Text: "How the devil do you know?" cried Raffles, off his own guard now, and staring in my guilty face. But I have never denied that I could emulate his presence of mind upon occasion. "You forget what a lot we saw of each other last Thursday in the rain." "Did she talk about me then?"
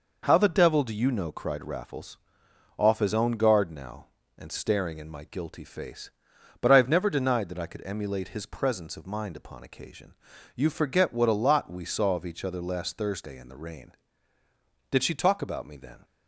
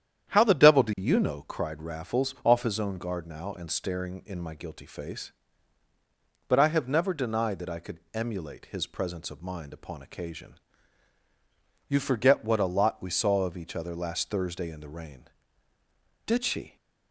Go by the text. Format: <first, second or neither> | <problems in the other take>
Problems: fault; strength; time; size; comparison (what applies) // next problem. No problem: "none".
first | starts louder than the rest; strong; until 1.3 s; 9.5 dB // stops before "talk about me then"; at 16.7 s